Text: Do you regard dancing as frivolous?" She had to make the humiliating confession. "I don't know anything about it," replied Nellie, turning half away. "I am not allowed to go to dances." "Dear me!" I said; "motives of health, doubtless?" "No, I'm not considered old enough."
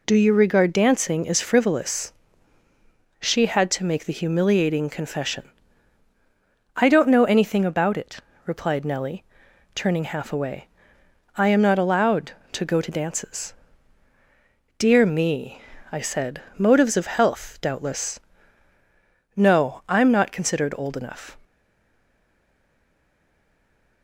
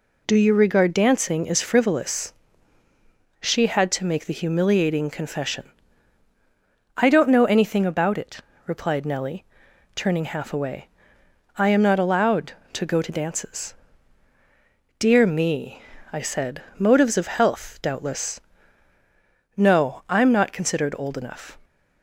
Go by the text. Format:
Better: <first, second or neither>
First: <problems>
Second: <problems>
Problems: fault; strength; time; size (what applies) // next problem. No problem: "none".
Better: second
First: stays silent after the last word; strong; from 21.4 s on; 2.6 s long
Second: none